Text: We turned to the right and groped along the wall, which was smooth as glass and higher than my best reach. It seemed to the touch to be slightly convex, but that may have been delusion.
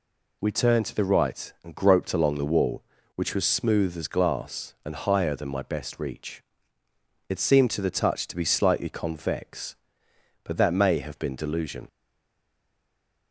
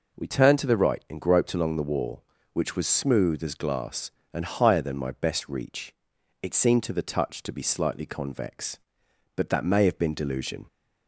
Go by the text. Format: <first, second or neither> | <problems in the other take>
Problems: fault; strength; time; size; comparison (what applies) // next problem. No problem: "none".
second | stays silent after the last word; noticeable; from 11.8 s on; 1.5 s long